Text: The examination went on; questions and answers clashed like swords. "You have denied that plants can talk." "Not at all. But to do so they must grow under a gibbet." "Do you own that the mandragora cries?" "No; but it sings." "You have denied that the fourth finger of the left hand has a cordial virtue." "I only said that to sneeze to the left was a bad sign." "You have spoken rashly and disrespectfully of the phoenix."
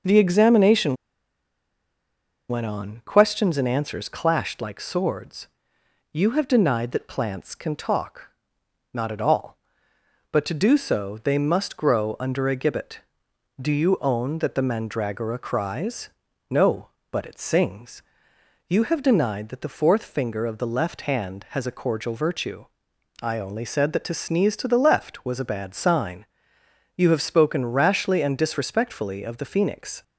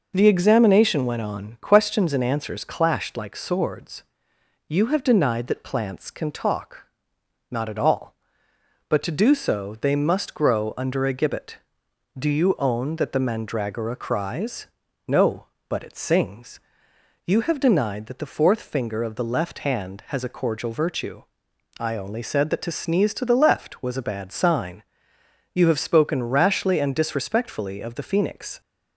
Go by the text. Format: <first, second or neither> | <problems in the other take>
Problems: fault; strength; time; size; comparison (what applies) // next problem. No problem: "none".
second | pauses between "examination" and "went"; strong; at 0.9 s; 1.5 s long